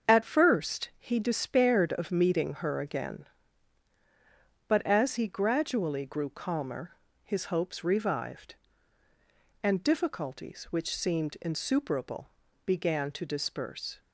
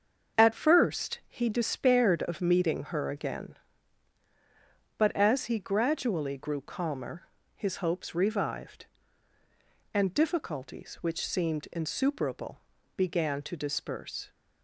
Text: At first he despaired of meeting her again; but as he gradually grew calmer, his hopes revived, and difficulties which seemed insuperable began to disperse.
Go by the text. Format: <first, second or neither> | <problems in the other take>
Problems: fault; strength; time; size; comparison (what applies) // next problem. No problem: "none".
neither | starts louder than the rest; the same in both // pauses between "insuperable" and "began"; slight; the same in both